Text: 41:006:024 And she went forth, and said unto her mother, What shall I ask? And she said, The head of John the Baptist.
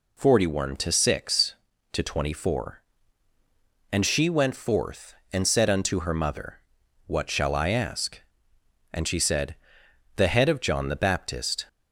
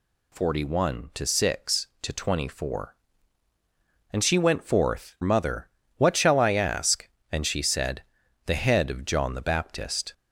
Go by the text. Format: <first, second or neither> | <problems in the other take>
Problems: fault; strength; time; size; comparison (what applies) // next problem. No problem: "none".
first | skips "and said unto her"; at 5.1 s